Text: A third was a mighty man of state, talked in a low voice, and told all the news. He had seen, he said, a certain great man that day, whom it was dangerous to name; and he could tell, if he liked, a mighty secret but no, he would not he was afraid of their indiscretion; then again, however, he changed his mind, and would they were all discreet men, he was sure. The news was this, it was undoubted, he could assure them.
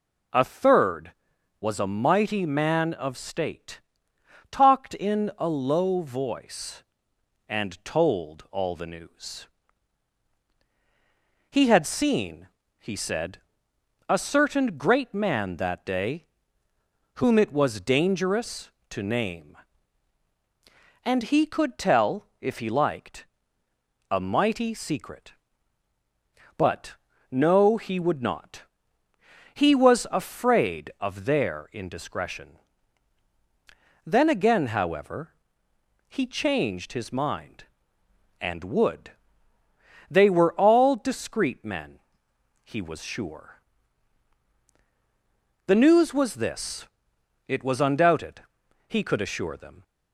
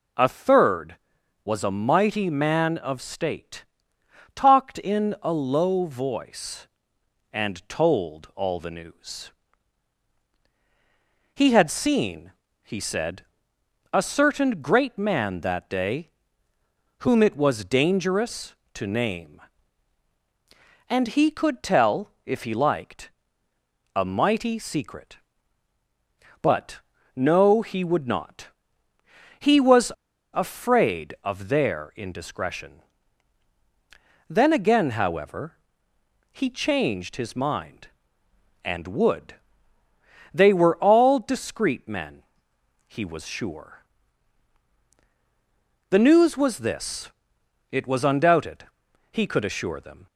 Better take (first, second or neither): first